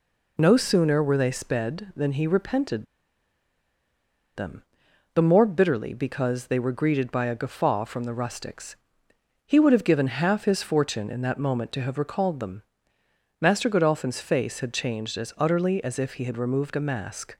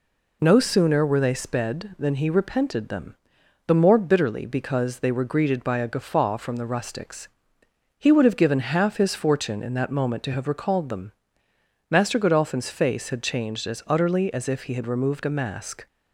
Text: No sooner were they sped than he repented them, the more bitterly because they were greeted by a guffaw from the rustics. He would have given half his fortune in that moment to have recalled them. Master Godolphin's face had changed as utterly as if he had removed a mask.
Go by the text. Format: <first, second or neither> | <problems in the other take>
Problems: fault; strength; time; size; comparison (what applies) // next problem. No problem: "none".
second | pauses between "repented" and "them"; strong; at 2.8 s; 1.5 s long